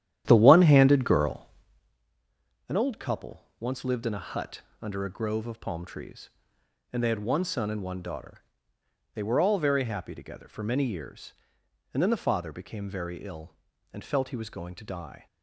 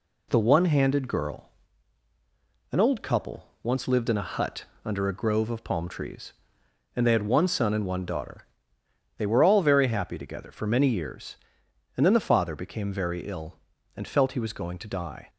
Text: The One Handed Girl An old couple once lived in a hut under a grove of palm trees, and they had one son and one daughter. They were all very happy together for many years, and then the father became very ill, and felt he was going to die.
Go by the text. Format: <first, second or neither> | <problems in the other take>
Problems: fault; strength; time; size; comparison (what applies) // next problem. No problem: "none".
second | starts louder than the rest; strong; until 2.0 s; 11 dB // pauses between "Girl" and "An"; at 1.4 s; 1.2 s long; also in the second // pauses between "couple" and "once"; slight; at 3.4 s; 0.16 s long; slight in the second // pauses between "hut" and "under"; slight; at 4.6 s; 0.20 s long; slight in the second